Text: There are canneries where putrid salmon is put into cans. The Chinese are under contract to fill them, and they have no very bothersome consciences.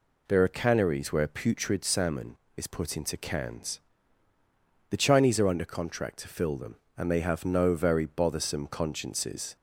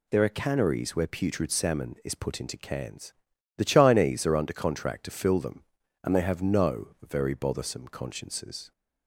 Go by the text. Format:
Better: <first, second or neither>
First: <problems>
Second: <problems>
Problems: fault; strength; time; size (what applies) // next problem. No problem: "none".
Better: neither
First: none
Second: none